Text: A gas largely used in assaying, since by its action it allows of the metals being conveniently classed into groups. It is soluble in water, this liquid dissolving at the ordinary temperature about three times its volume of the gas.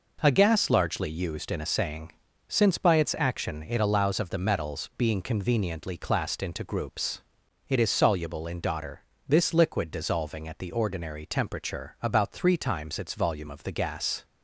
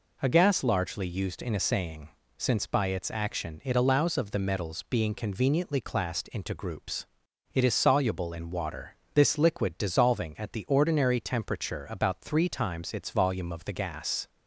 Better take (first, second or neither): second